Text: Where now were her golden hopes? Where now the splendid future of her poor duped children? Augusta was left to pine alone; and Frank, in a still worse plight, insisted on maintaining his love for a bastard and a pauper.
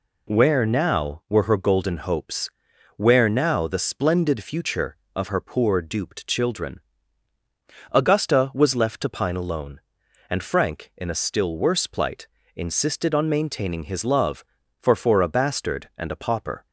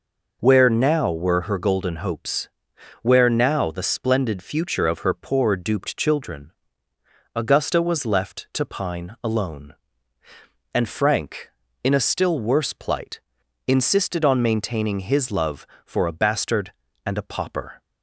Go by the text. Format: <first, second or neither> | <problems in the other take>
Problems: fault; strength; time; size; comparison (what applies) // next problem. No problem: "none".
second | says "for" twice; at 14.9 s